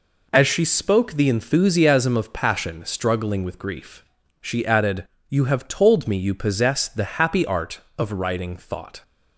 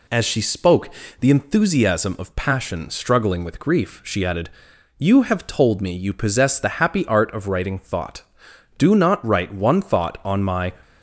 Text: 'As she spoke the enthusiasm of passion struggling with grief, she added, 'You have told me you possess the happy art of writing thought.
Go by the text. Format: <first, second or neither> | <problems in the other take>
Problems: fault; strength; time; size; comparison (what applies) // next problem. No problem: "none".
first | pauses between "spoke" and "the"; slight; at 0.8 s; 0.30 s long // goes on to say "Do not write one thought on my"; strong; from 8.7 s on; 1.9 s long